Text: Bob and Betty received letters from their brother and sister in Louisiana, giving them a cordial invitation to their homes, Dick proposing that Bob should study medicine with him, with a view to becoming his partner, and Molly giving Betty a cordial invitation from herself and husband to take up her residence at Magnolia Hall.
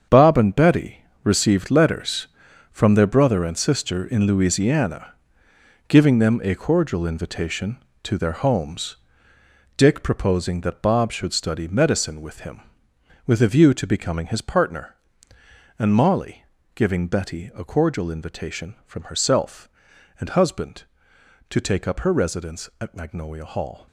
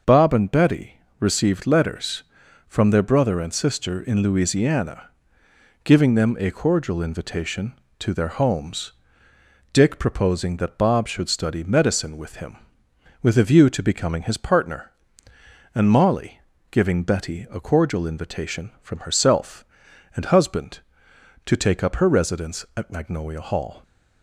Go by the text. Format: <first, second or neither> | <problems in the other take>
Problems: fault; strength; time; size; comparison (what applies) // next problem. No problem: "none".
second | gets quieter; strong; throughout; 10.5 dB // pauses between "Betty" and "received"; slight; at 1.0 s; 0.18 s long; slight in the second // pauses between "Molly" and "giving"; slight; at 16.4 s; 0.30 s long; slight in the second